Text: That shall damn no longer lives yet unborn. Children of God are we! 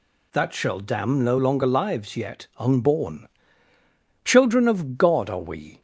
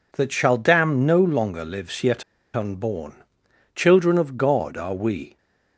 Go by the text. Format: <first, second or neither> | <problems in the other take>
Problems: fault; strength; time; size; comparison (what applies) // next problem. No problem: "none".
first | pauses between "yet" and "unborn"; slight; at 2.2 s; 0.31 s long